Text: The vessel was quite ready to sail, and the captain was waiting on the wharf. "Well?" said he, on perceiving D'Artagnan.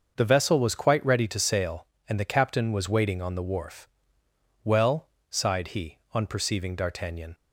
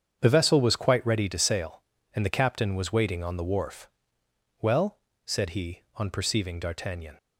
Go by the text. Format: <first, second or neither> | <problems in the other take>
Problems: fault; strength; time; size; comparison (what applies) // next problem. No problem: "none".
second | starts louder than the rest; until 1.1 s; 6.5 dB; strong in the second // says "sighed" for "said"; at 5.2 s